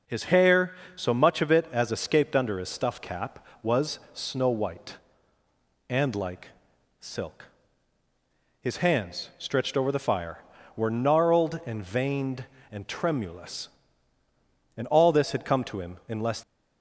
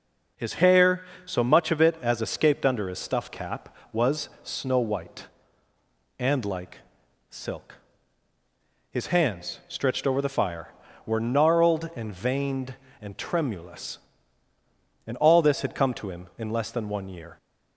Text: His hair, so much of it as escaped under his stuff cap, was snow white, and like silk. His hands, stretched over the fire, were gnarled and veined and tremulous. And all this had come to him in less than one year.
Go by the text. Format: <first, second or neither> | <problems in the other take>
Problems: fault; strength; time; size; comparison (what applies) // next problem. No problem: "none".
second | pauses between "like" and "silk"; noticeable; at 6.4 s; 0.50 s long; noticeable in the second // stops before "than one year"; at 16.4 s